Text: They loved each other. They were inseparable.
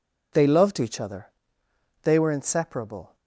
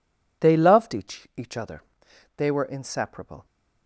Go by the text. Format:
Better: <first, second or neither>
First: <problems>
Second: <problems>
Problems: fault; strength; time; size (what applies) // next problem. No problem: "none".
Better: first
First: none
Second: says "each" twice; at 1.3 s